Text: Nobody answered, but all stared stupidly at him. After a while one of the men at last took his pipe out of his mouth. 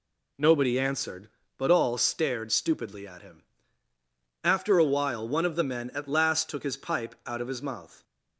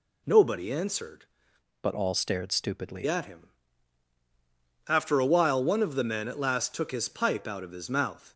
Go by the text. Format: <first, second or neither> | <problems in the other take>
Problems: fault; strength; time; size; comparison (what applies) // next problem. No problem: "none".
first | changes voice from "but" to "stupidly"; from 1.8 to 3.0 s; 1.2 s long